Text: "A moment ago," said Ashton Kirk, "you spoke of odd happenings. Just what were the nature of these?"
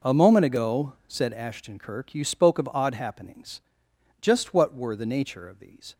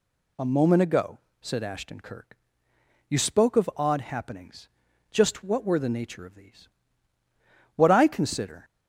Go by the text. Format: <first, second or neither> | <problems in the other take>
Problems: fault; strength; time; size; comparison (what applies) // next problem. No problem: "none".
first | goes on to say "What I consider"; noticeable; from 7.7 s on; 0.88 s long